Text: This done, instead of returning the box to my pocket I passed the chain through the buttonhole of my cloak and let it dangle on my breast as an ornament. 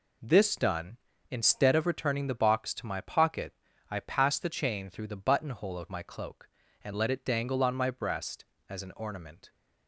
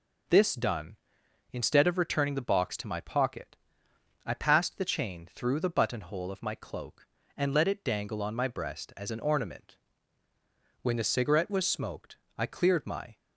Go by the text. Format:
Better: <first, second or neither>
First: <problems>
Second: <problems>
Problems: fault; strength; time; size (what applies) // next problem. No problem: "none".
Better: first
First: pauses between "pocket" and "I"; at 3.5 s; 0.38 s long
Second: pauses between "pocket" and "I"; noticeable; at 3.5 s; 0.68 s long // goes on to say "When the cigarette was smoked I cleared my"; strong; from 10.8 s on; 2.3 s long